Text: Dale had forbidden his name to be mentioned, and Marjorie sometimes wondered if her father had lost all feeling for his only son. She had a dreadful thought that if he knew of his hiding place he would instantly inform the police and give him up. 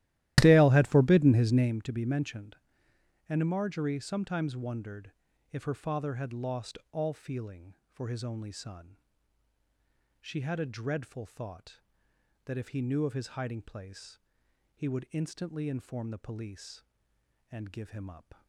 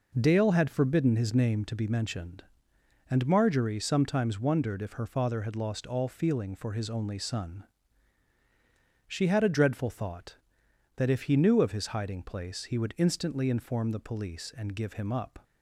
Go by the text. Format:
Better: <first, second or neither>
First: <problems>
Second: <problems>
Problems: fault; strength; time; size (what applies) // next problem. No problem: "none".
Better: second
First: starts louder than the rest; strong; until 1.7 s; 14.5 dB // pauses between "wondered" and "if"; at 5.1 s; 0.40 s long // pauses between "lost" and "all"; slight; at 6.7 s; 0.16 s long // pauses between "place" and "he"; noticeable; at 14.1 s; 0.56 s long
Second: none